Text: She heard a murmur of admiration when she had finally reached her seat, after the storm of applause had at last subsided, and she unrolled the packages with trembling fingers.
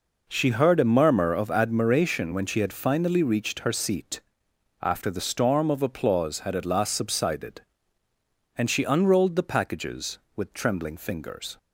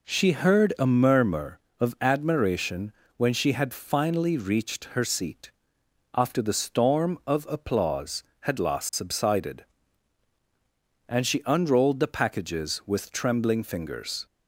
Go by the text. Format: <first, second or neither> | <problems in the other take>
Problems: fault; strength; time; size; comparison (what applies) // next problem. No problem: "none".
first | pauses between "admiration" and "when"; slight; at 2.9 s; 0.24 s long // skips "at"; at 8.5 s